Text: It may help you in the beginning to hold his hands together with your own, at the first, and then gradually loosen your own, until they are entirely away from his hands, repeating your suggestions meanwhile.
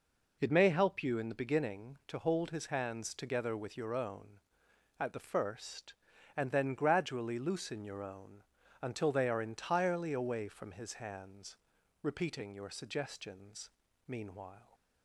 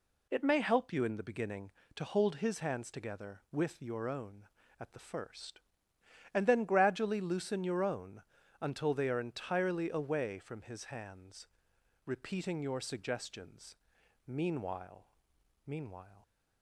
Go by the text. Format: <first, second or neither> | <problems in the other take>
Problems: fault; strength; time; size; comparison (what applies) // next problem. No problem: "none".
first | pauses between "suggestions" and "meanwhile"; noticeable; at 13.7 s; 0.52 s long; slight in the first // says "meanwhile" twice; at 15.6 s